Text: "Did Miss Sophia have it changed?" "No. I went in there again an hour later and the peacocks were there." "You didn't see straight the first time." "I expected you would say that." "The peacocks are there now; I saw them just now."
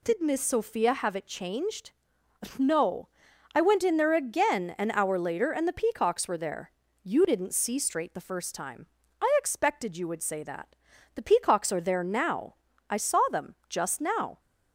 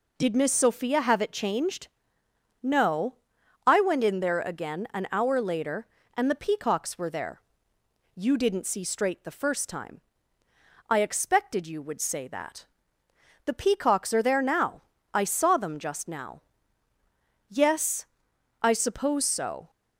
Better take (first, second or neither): first